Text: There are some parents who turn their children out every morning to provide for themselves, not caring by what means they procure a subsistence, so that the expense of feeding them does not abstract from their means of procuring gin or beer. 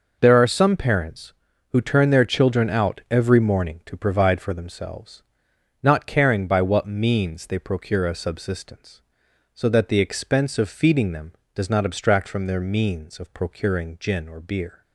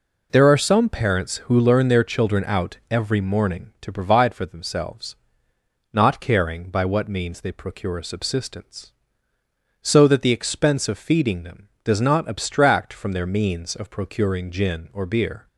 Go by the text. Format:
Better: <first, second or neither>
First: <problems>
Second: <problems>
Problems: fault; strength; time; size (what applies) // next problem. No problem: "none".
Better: first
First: none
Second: says "learn" for "turn"; at 1.5 s